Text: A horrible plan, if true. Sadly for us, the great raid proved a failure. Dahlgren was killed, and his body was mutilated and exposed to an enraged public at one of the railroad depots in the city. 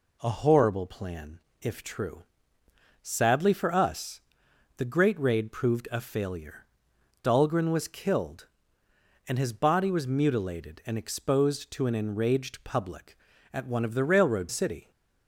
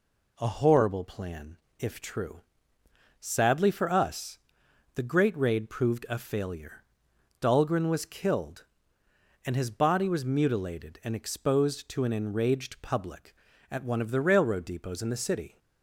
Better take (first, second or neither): second